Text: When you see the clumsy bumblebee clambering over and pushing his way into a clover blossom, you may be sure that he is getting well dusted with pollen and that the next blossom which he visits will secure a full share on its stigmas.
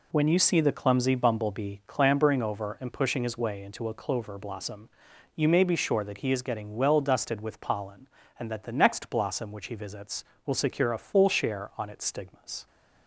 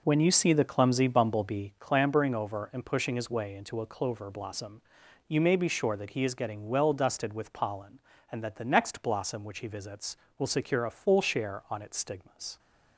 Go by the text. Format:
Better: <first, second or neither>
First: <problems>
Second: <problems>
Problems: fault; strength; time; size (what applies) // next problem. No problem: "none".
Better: first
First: none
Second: starts louder than the rest; noticeable; until 1.8 s; 4.5 dB